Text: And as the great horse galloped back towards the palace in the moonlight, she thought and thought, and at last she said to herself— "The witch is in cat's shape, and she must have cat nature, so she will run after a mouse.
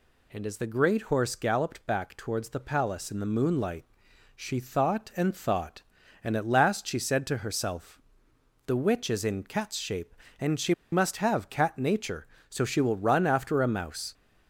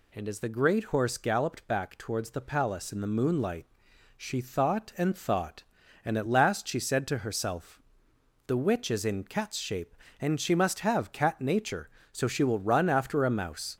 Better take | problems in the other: second | pauses between "she" and "must"; slight; at 10.7 s; 0.18 s long

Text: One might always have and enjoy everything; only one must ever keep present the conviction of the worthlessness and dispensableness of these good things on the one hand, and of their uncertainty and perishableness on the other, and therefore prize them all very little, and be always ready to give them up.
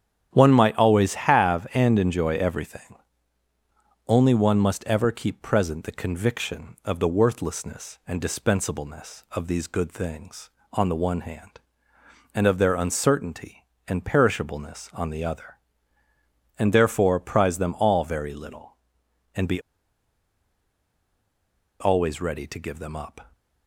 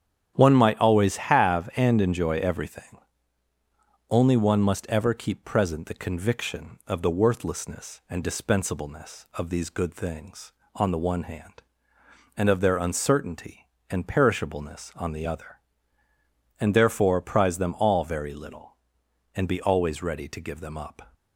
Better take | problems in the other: second | starts louder than the rest; strong; until 1.3 s; 9.5 dB; strong in the second // pauses between "be" and "always"; strong; at 19.5 s; 2.2 s long

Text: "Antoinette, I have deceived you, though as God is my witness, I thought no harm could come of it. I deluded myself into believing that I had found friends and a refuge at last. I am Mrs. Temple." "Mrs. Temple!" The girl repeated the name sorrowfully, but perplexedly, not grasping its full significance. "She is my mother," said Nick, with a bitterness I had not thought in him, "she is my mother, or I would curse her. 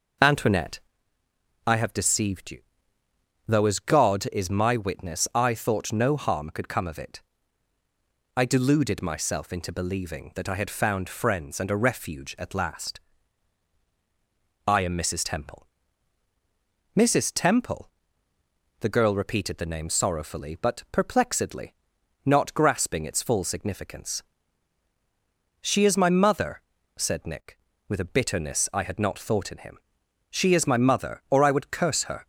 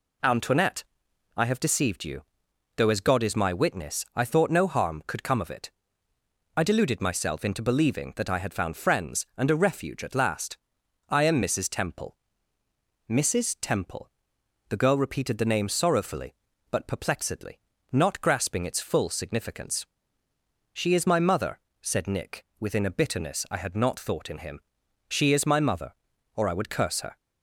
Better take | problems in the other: first | says "within" for "with"; at 22.5 s

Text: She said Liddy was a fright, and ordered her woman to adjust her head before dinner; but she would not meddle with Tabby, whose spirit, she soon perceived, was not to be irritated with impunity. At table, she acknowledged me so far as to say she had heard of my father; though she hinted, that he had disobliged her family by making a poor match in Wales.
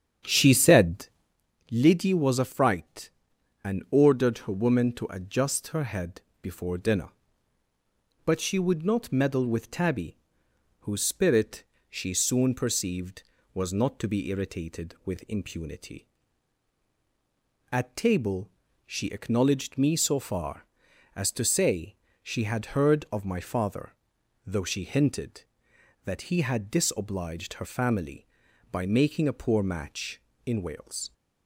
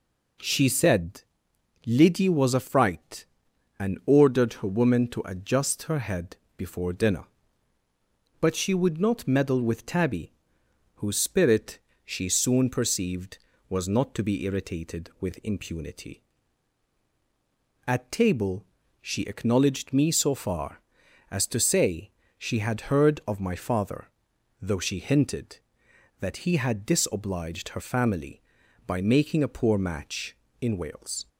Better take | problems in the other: second | starts louder than the rest; strong; until 1.4 s; 8.5 dB // pauses between "said" and "Liddy"; noticeable; at 1.0 s; 0.64 s long; noticeable in the second // pauses between "head" and "before"; slight; at 6.2 s; 0.20 s long; slight in the second // pauses between "say" and "she"; slight; at 21.9 s; 0.28 s long; slight in the second

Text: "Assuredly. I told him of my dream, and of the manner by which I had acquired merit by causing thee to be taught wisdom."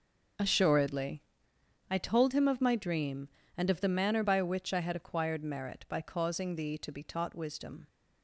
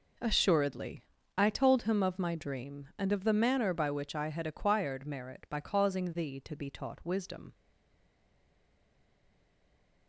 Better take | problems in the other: first | stays silent after the last word; strong; from 7.5 s on; 2.5 s long

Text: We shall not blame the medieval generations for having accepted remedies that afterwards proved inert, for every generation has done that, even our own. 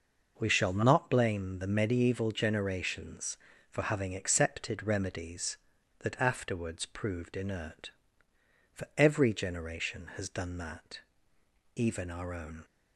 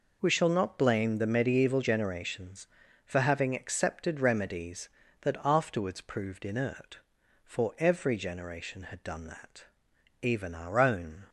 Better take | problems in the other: first | says "had" for "has"; at 8.8 s

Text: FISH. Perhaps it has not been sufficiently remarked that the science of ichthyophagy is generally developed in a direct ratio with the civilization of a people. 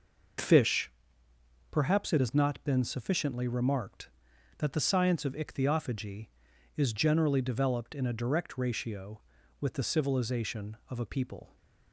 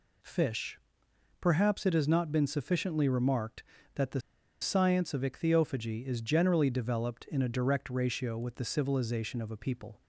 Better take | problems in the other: first | pauses between "the" and "science"; at 4.2 s; 0.40 s long

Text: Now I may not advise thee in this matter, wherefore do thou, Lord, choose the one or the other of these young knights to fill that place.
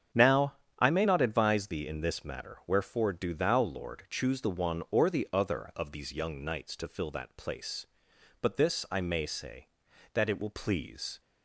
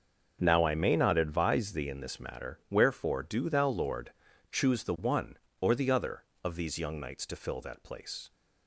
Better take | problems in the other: second | starts louder than the rest; strong; until 1.3 s; 8 dB; also in the second // pauses between "Now" and "I"; slight; at 0.5 s; 0.22 s long // goes on to say "But this I may say that it will please"; strong; from 8.4 s on; 2.8 s long

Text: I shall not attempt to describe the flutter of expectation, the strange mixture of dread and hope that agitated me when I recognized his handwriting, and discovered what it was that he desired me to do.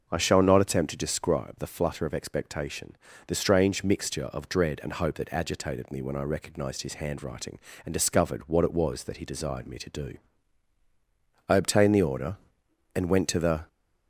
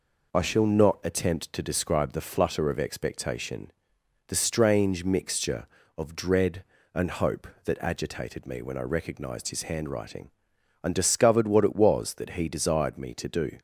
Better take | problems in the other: second | starts louder than the rest; until 1.1 s; 6 dB // goes on to say "I obtained the order and went to the"; strong; from 11.4 s on; 2.1 s long

